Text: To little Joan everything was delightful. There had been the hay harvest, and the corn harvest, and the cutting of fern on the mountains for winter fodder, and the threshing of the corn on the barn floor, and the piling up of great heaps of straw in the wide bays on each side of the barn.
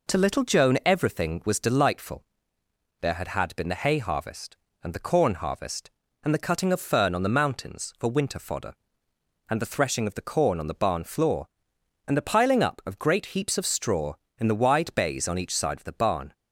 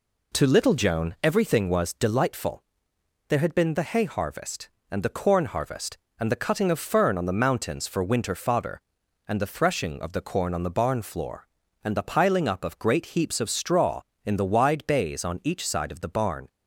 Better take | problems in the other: second | says "had" twice; at 3.2 s

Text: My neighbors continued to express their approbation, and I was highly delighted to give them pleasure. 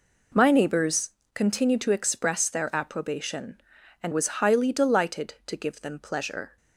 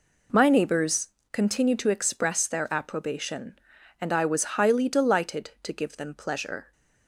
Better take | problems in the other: second | pauses between "neighbors" and "continued"; slight; at 1.1 s; 0.24 s long; slight in the second // skips "I"; at 4.1 s

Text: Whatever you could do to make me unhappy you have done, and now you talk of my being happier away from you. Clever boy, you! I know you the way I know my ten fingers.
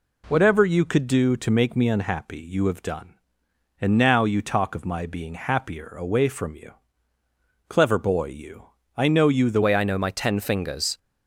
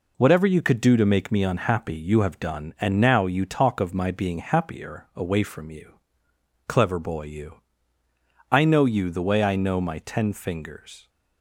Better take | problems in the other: second | changes voice at "way"; from 9.6 s on; 1.3 s long

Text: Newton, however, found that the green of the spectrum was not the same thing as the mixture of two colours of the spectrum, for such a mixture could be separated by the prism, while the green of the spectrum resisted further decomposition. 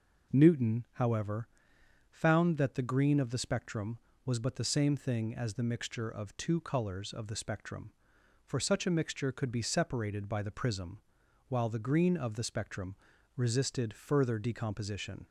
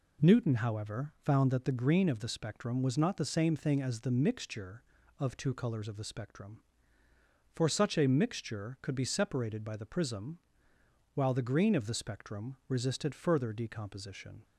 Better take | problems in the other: second | says "but" for "not"; at 4.3 s // pauses between "spectrum" and "resisted"; at 12.9 s; 0.40 s long

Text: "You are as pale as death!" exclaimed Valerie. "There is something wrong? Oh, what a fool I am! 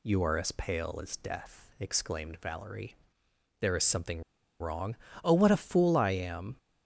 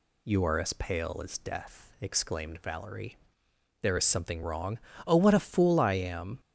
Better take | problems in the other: second | pauses between "something" and "wrong"; at 4.2 s; 0.38 s long

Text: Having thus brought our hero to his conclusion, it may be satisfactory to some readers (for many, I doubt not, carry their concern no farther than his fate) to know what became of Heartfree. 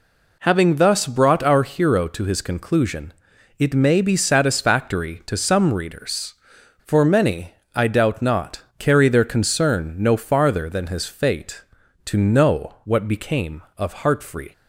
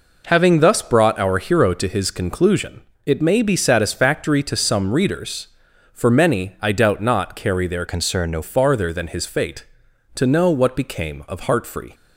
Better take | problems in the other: first | changes voice from "concern" to "no"; from 7.8 to 8.4 s; 0.6 s long

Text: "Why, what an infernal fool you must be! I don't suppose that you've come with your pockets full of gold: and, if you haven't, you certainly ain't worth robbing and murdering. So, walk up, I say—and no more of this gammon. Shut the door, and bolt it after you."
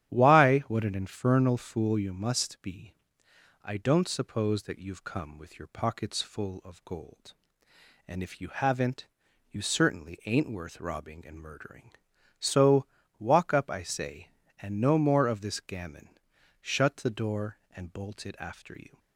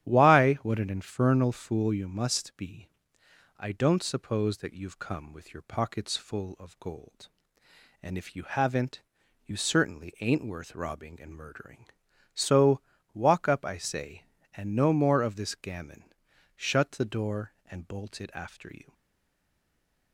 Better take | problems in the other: first | starts louder than the rest; strong; until 1.1 s; 11 dB; strong in the first // stays silent after the last word; noticeable; from 18.9 s on; 1.2 s long

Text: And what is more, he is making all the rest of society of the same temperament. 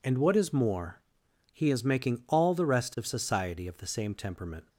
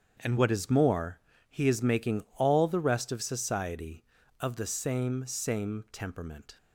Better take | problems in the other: first | starts louder than the rest; strong; until 1.5 s; 7.5 dB // says "same" twice; at 5.2 s

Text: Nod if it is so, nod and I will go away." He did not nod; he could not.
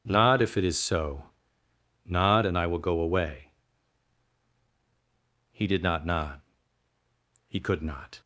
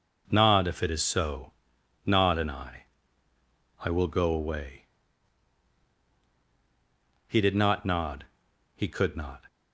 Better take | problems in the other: first | says "I" twice; at 3.8 s

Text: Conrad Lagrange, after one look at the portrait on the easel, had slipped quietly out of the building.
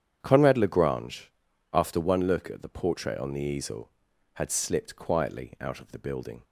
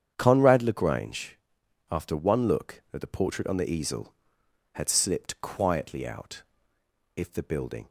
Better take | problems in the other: first | starts louder than the rest; strong; until 1.1 s; 8.5 dB; strong in the first // says "if" for "of"; at 7.1 s

